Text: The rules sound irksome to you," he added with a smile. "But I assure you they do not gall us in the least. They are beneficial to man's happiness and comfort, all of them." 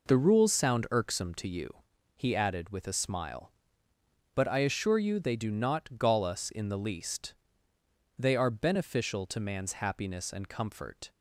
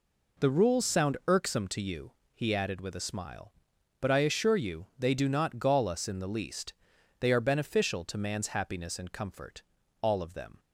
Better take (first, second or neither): second